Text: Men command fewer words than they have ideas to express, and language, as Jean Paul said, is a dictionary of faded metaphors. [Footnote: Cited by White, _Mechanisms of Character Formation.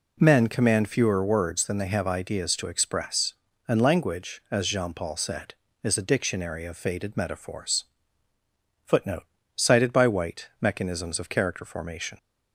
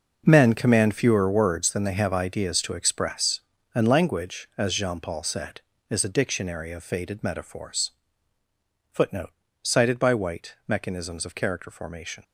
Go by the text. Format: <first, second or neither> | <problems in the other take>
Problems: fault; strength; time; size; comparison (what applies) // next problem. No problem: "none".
first | gets quieter; strong; throughout; 12 dB